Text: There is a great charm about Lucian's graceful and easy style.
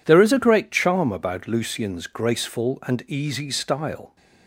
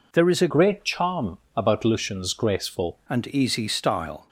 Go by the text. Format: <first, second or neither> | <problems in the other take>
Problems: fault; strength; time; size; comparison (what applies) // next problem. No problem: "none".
first | changes voice from "great" to "graceful"; from 0.5 to 2.9 s; 2.4 s long // pauses between "charm" and "about"; slight; at 1.3 s; 0.18 s long